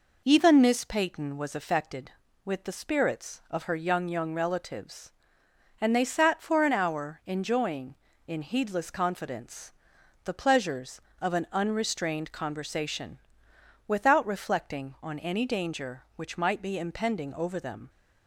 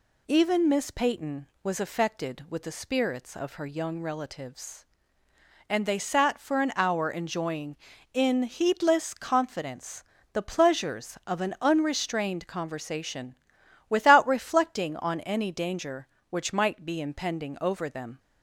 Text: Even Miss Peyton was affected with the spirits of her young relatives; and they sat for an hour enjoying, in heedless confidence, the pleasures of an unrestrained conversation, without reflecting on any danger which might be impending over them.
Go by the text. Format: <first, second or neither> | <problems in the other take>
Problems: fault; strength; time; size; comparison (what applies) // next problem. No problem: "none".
second | says "young" twice; at 4.0 s